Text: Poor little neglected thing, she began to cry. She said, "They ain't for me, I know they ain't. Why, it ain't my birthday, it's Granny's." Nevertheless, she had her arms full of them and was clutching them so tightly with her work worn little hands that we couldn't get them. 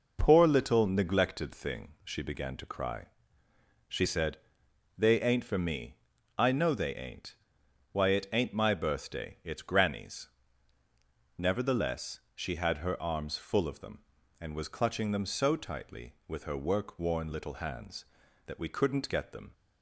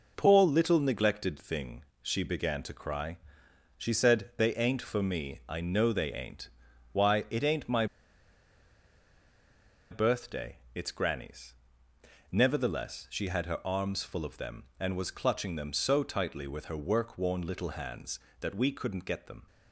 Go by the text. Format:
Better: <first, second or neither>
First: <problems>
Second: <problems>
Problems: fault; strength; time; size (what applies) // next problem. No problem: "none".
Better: first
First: none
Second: pauses between "my" and "birthday"; strong; at 7.8 s; 2.0 s long